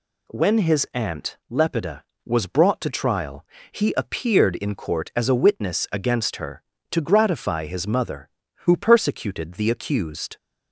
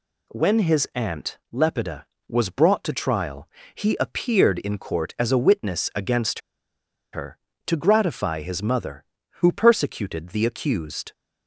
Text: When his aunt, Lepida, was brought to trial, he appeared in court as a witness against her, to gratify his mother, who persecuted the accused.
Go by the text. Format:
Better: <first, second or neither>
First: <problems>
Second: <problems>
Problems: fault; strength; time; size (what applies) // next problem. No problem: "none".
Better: first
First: none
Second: pauses between "against" and "her"; noticeable; at 6.3 s; 0.73 s long